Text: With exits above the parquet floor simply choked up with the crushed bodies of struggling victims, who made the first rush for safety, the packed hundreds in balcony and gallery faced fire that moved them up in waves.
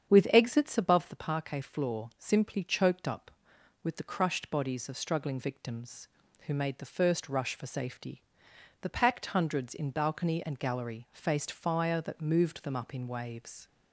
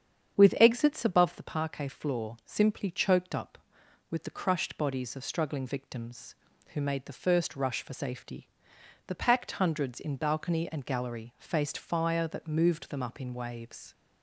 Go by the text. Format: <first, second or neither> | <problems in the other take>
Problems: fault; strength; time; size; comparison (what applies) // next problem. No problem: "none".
neither | starts louder than the rest; strong; the same in both